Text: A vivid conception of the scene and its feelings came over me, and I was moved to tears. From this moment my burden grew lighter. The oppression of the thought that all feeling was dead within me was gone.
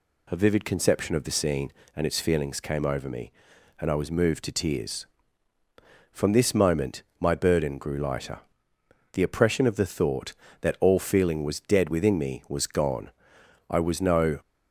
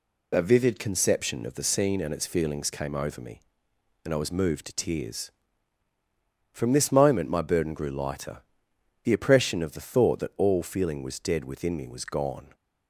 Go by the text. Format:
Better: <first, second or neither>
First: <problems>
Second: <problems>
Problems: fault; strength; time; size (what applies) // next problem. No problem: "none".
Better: second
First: pauses between "moment" and "my"; slight; at 7.0 s; 0.16 s long // goes on to say "I was no"; noticeable; from 13.6 s on; 0.70 s long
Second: none